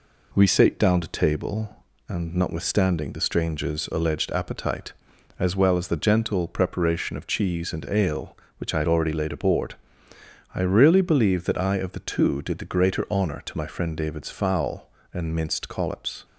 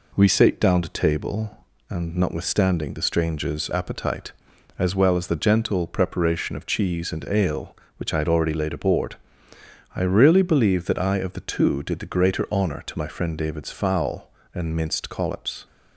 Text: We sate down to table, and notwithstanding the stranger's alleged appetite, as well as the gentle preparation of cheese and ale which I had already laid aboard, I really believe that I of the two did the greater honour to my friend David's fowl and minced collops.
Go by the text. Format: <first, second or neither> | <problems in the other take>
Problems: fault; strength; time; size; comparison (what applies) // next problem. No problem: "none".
first | skips "alleged"; at 3.6 s